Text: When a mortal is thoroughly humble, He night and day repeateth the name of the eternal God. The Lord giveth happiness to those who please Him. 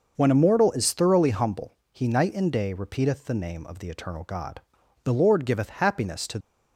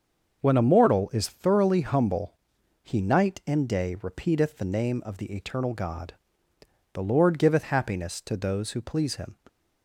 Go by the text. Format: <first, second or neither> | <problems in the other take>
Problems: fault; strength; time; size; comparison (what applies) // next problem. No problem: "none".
second | starts louder than the rest; noticeable; until 1.1 s; 6 dB; also in the second // stops before "those who please Him"; at 6.4 s